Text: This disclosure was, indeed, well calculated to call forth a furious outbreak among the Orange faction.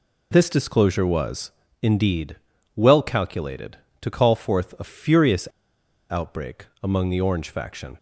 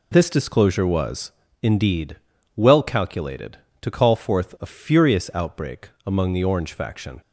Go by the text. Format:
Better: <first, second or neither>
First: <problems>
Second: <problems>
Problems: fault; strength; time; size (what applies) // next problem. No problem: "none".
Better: second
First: pauses between "furious" and "outbreak"; noticeable; at 5.4 s; 0.64 s long // pauses between "outbreak" and "among"; slight; at 6.6 s; 0.18 s long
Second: pauses between "outbreak" and "among"; slight; at 5.8 s; 0.18 s long